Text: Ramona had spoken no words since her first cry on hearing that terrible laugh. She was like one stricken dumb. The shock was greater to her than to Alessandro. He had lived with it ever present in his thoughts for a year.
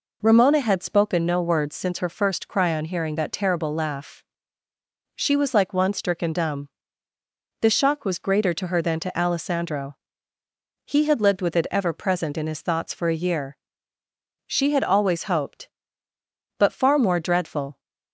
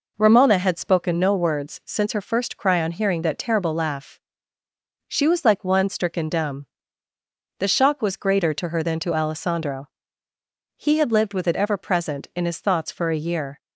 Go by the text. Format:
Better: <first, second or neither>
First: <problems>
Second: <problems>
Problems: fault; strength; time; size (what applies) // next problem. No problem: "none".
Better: second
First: goes on to say "She had always hoped But far more dreadful"; strong; from 14.4 s on; 3.3 s long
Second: none